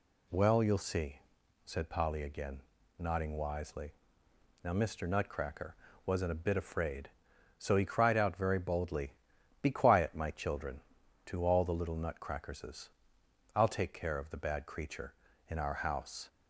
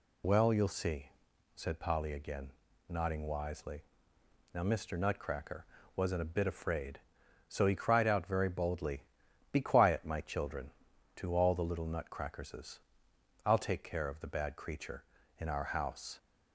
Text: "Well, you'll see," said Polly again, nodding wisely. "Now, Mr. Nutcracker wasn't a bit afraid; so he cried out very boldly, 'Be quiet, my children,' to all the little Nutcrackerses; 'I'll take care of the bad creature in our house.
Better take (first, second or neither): first